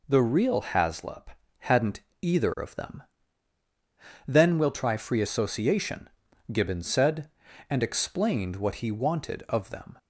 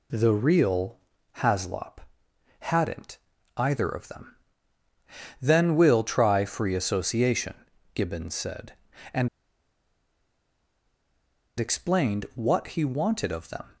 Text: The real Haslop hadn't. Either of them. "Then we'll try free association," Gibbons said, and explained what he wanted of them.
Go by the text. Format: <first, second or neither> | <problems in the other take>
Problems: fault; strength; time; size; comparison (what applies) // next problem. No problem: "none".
first | pauses between "real" and "Haslop"; at 0.9 s; 0.40 s long // pauses between "Haslop" and "hadn't"; noticeable; at 1.9 s; 0.60 s long; slight in the first // pauses between "and" and "explained"; strong; at 9.2 s; 2.3 s long